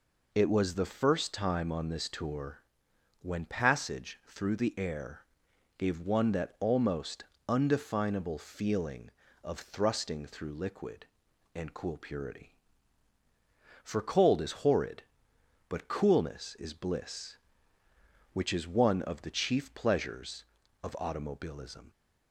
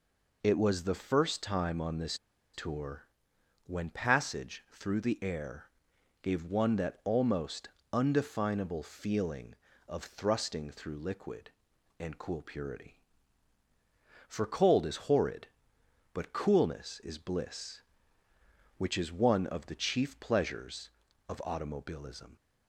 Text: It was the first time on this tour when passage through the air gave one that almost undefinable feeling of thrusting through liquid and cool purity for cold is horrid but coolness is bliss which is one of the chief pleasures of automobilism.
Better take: first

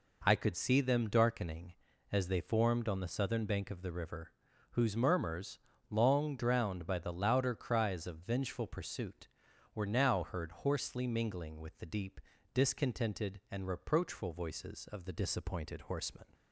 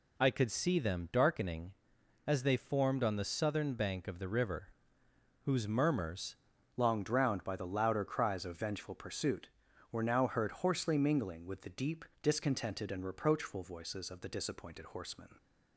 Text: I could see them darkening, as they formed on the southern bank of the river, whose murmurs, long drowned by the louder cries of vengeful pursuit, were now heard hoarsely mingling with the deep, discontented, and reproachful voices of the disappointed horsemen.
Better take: first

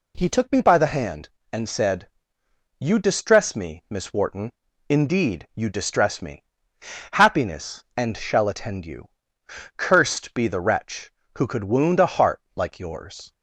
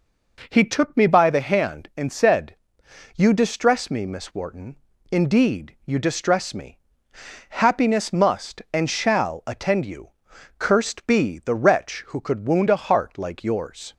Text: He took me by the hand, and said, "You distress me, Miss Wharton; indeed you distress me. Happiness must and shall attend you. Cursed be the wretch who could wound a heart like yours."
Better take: second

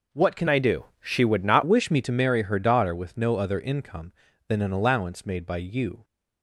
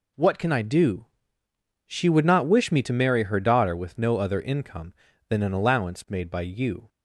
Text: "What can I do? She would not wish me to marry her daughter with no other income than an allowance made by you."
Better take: second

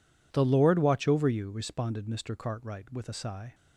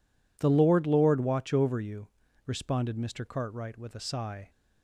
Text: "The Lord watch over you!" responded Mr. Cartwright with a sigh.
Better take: first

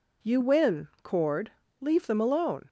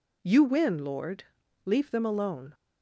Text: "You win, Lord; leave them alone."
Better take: second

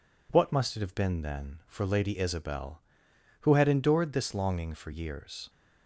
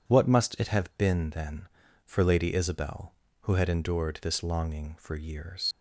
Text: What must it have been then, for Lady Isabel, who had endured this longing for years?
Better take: first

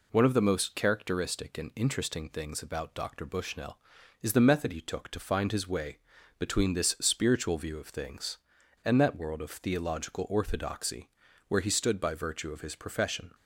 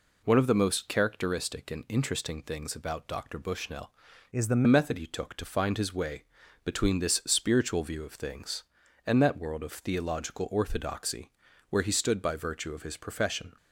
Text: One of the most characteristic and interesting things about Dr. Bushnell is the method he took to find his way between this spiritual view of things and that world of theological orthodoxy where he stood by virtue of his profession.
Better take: first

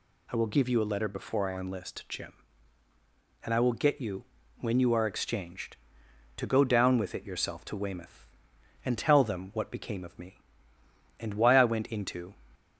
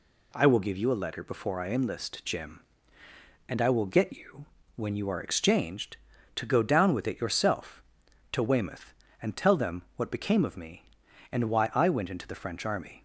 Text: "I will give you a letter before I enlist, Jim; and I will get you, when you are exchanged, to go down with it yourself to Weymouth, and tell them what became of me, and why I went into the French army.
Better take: second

